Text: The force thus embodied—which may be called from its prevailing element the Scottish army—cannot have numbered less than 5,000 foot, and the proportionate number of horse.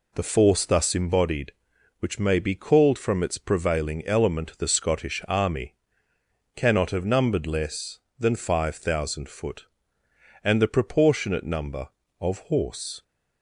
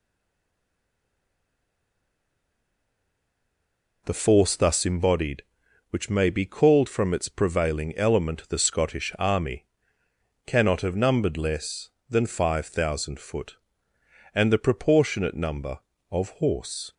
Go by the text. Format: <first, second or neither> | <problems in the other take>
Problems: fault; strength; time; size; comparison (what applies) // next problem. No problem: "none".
first | stays silent before the first word; strong; until 4.0 s; 4.0 s long